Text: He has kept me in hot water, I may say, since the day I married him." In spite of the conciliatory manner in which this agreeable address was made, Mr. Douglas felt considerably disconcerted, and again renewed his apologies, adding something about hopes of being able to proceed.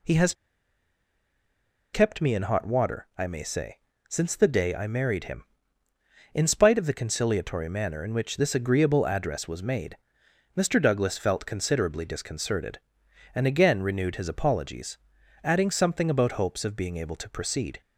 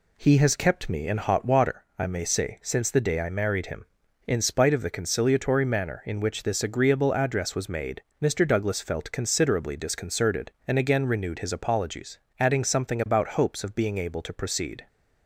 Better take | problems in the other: second | pauses between "has" and "kept"; strong; at 0.3 s; 1.6 s long

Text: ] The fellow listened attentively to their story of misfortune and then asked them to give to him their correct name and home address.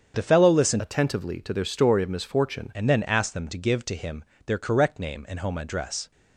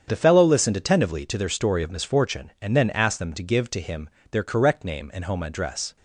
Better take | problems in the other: second | starts louder than the rest; strong; until 1.1 s; 7.5 dB; strong in the second // changes voice from "attentively" to "misfortune"; from 0.7 to 2.7 s; 2.0 s long // pauses between "him" and "their"; slight; at 4.2 s; 0.22 s long; slight in the second

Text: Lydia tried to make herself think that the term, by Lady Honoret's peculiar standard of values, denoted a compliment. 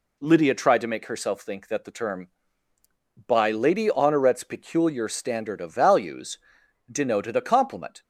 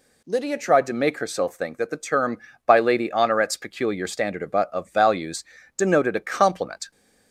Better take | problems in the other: first | says "of" twice; at 4.5 s

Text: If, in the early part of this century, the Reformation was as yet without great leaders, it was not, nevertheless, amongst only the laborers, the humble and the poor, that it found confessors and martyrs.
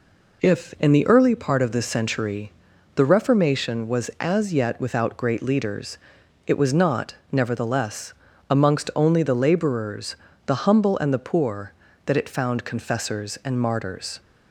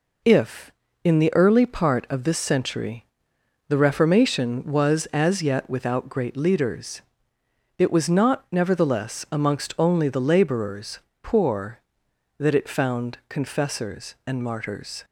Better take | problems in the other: first | skips "the humble and the"; at 11.1 s

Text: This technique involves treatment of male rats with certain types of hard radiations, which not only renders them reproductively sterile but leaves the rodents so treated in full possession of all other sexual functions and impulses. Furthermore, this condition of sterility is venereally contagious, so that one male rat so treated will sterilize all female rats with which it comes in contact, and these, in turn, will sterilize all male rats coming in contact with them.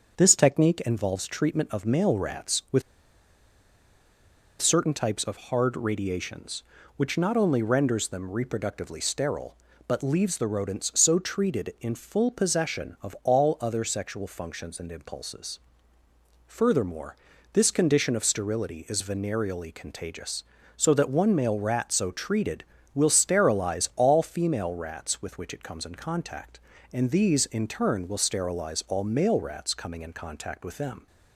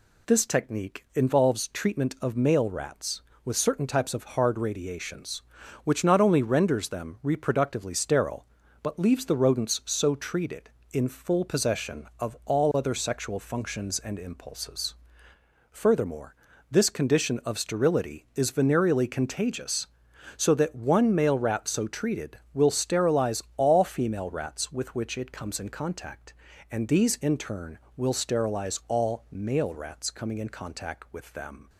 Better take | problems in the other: second | starts louder than the rest; until 1.1 s; 7 dB // pauses between "with" and "certain"; strong; at 2.8 s; 1.7 s long

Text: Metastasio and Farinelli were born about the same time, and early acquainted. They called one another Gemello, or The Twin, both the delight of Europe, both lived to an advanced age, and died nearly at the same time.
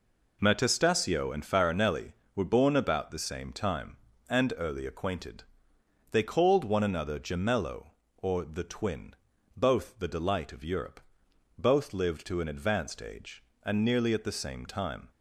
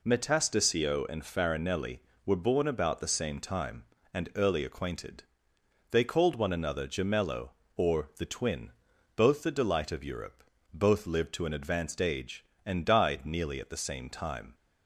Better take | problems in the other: second | skips "died"; at 13.8 s

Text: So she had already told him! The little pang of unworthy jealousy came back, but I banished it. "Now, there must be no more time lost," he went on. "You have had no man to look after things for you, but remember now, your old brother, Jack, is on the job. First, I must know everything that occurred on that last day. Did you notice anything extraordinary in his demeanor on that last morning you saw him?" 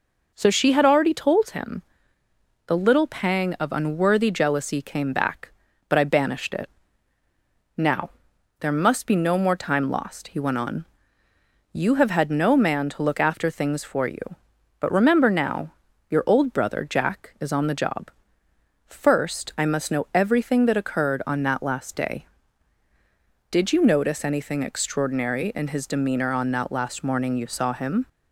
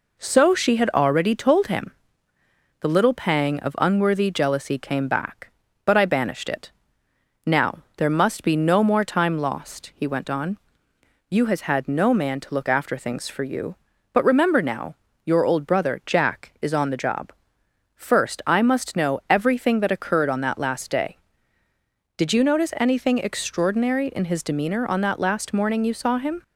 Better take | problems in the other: first | says "has" for "have"; at 11.4 s

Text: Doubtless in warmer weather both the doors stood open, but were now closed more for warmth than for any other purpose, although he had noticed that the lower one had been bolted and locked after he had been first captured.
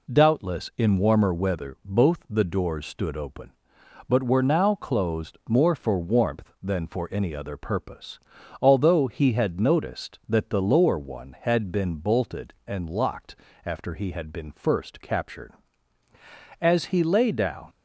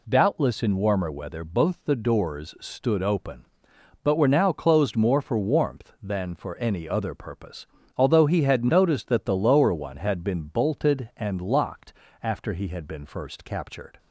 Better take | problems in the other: second | pauses between "locked" and "after"; slight; at 13.3 s; 0.30 s long; slight in the second // goes on to say "As he lay down"; noticeable; from 16.5 s on; 1.1 s long

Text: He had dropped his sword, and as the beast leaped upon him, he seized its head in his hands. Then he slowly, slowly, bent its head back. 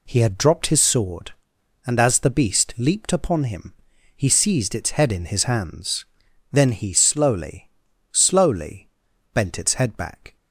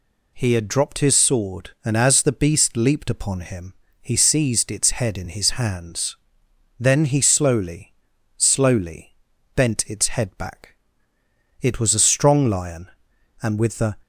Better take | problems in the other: first | goes on to say "It was a strong lion and with the"; strong; from 11.6 s on; 2.3 s long

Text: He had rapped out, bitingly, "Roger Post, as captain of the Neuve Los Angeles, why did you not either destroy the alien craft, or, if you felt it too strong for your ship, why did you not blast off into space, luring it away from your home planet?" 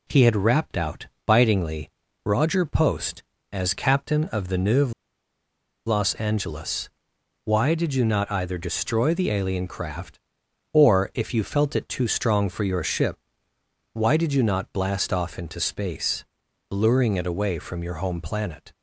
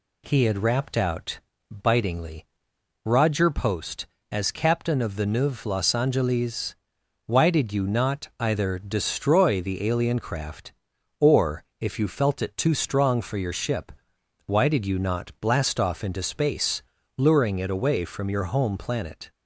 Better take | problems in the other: second | pauses between "Neuve" and "Los"; noticeable; at 4.9 s; 0.94 s long

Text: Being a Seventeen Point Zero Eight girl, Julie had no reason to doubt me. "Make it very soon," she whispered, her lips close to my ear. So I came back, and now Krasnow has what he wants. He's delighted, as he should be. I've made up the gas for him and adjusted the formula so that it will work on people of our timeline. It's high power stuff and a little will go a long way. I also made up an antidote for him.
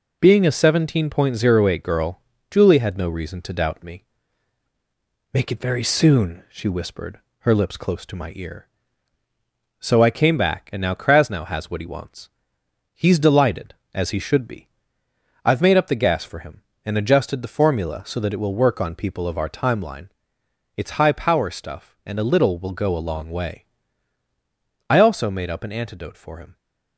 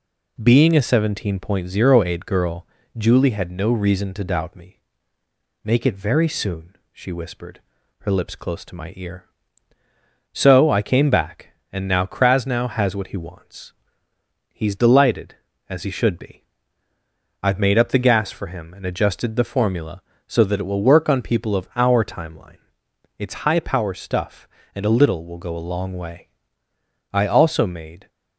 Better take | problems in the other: first | stops before "up an antidote for him"; at 28.0 s

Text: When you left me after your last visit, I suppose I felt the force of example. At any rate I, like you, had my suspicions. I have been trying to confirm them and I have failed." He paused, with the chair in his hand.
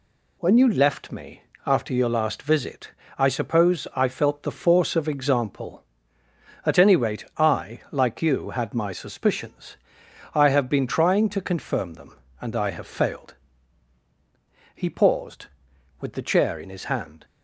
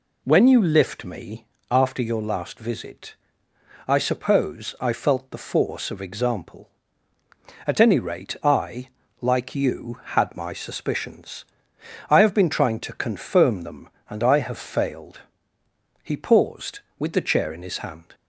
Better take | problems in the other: first | says "lift" for "left"; at 0.6 s // pauses between "me" and "after"; slight; at 1.4 s; 0.22 s long; slight in the first

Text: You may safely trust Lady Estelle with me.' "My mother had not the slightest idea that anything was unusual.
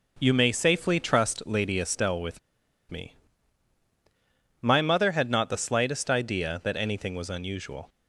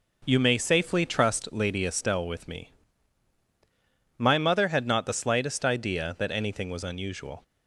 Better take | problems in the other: second | pauses between "with" and "me"; noticeable; at 2.3 s; 0.51 s long

